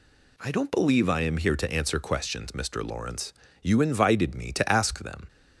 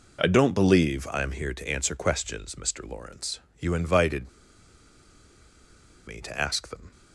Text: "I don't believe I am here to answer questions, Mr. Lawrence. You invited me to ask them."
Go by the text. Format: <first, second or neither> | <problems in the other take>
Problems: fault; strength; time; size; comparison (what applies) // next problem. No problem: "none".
first | pauses between "invited" and "me"; strong; at 4.2 s; 1.7 s long